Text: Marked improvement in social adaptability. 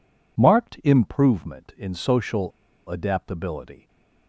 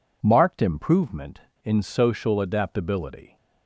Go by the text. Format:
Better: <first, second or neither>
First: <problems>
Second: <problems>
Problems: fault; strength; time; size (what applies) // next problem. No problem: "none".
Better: second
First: pauses between "social" and "adaptability"; at 2.5 s; 0.38 s long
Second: none